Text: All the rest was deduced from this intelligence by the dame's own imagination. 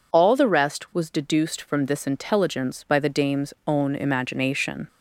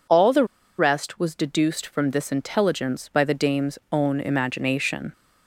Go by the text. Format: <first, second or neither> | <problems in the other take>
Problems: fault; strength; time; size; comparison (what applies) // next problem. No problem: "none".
first | pauses between "the" and "rest"; slight; at 0.4 s; 0.32 s long